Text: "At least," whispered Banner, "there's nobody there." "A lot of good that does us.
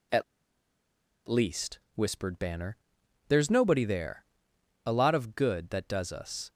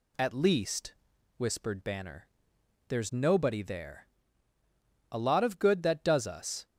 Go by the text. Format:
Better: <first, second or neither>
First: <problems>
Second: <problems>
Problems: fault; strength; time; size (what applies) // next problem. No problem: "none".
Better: second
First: pauses between "At" and "least"; at 0.2 s; 1.0 s long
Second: none